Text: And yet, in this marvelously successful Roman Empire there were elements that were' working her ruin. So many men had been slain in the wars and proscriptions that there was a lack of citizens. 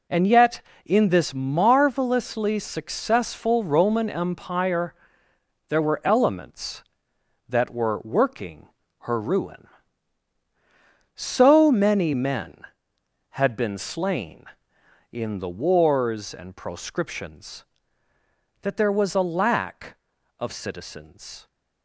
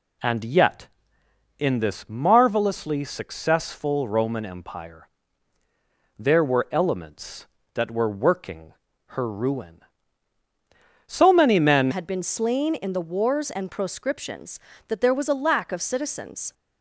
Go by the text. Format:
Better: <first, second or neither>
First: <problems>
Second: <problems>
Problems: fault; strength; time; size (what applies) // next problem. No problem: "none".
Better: first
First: pauses between "Empire" and "there"; noticeable; at 4.9 s; 0.74 s long // pauses between "working" and "her"; slight; at 8.6 s; 0.32 s long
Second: pauses between "Empire" and "there"; at 5.0 s; 1.1 s long // pauses between "working" and "her"; slight; at 8.7 s; 0.36 s long // changes voice at "had"; from 11.9 s on; 4.6 s long